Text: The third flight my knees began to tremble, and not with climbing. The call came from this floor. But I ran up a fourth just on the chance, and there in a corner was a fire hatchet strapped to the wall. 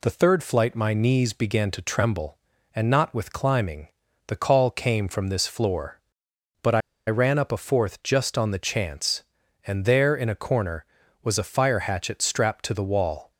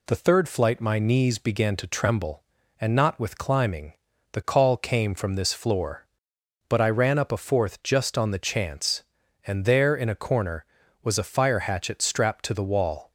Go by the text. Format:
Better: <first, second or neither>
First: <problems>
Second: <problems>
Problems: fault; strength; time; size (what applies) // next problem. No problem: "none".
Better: second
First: pauses between "I" and "ran"; slight; at 6.8 s; 0.28 s long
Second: none